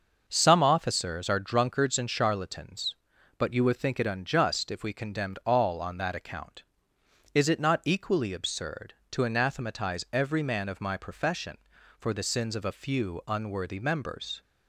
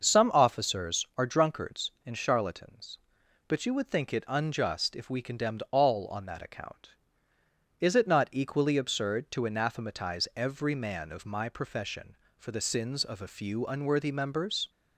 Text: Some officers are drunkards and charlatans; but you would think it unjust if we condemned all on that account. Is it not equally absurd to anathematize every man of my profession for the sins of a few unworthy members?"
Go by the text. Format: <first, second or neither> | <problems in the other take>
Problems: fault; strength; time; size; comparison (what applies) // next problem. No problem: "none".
neither | starts louder than the rest; noticeable; the same in both